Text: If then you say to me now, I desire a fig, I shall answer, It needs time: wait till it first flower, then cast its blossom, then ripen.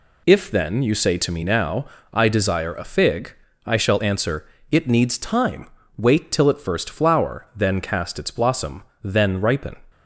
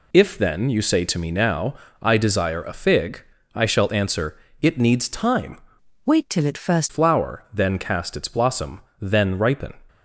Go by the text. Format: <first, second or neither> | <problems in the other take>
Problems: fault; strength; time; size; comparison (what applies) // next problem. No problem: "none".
first | changes voice from "wait" to "first"; from 6.0 to 6.9 s; 0.9 s long